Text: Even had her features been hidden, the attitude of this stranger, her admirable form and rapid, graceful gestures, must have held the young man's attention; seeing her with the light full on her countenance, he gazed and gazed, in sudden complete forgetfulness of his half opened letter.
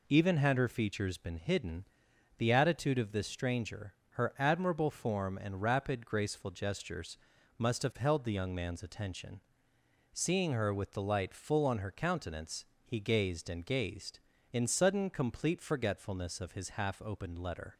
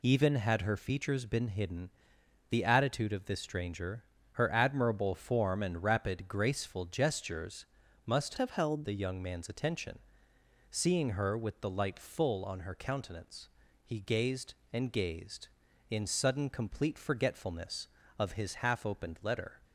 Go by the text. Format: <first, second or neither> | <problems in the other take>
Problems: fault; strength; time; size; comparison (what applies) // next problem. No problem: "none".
first | changes voice from "have" to "held"; from 8.3 to 8.8 s; 0.5 s long